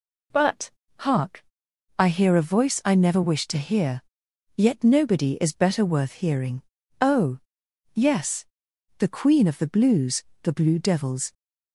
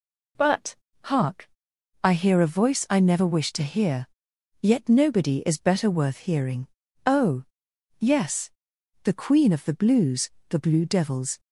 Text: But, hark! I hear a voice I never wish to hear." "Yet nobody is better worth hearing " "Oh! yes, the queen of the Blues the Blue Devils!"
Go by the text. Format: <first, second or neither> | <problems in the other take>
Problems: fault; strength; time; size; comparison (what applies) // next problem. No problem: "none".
neither | pauses between "Blues" and "the"; slight; the same in both